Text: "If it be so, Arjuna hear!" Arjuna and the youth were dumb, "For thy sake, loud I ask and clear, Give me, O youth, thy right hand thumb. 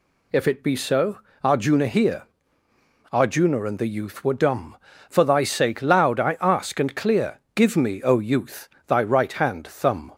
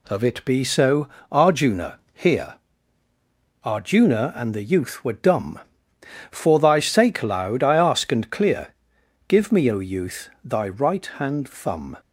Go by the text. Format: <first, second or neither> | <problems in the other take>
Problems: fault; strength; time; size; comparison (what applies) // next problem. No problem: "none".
first | says "Of" for "If"; at 0.0 s // pauses between "Arjuna" and "hear"; slight; at 1.9 s; 0.16 s long